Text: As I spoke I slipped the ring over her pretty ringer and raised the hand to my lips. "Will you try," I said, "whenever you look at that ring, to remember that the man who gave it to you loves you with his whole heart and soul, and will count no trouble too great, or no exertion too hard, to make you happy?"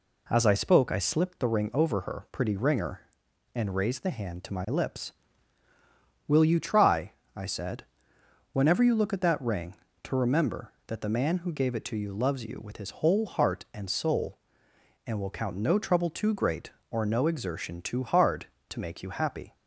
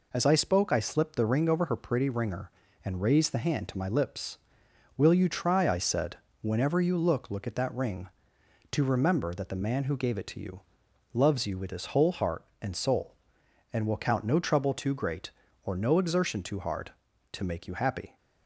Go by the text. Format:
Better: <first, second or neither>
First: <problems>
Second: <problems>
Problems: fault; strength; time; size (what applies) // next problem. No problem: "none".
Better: first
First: none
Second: says "look" twice; at 7.2 s // pauses between "you" and "loves"; noticeable; at 10.6 s; 0.52 s long